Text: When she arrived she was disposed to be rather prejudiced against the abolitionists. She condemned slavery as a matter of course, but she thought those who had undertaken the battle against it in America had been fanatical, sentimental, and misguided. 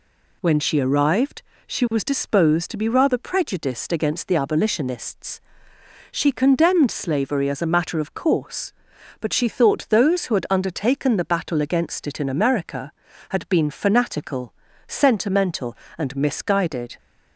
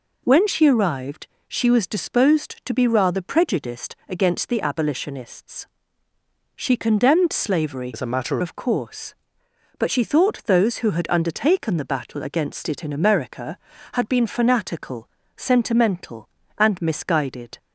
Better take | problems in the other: first | pauses between "arrived" and "she"; slight; at 1.2 s; 0.22 s long; slight in the first // changes voice from "as" to "matter"; from 7.9 to 8.3 s; 0.4 s long

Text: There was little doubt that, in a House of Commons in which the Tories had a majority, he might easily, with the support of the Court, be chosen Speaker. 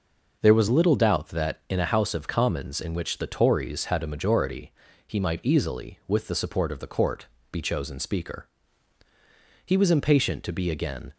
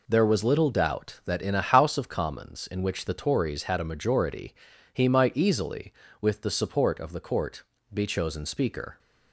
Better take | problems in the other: second | goes on to say "He was impatient to be again"; from 9.6 s on; 1.4 s long

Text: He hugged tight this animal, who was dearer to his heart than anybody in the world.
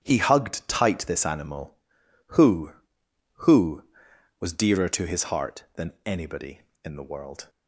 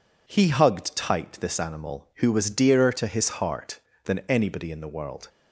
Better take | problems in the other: second | starts louder than the rest; strong; until 1.0 s; 9.5 dB // says "who" twice; at 3.3 s

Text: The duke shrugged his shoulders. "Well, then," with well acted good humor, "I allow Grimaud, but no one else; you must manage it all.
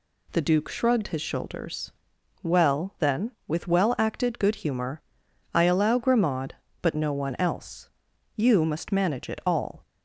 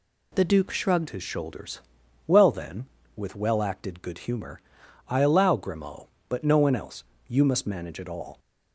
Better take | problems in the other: first | changes voice at "his"; from 1.0 s on; 7.3 s long

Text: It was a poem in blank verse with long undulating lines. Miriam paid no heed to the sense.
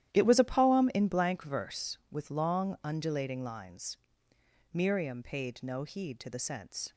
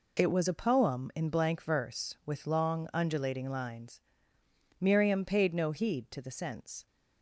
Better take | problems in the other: second | gets quieter; strong; throughout; 13.5 dB

